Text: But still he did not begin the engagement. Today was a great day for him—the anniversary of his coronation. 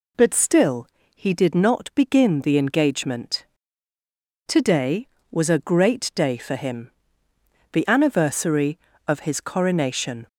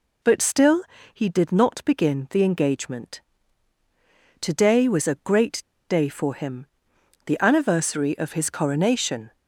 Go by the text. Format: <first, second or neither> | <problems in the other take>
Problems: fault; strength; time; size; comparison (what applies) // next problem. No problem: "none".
first | pauses between "still" and "he"; slight; at 0.8 s; 0.32 s long; slight in the first // pauses between "great" and "day"; slight; at 5.6 s; 0.25 s long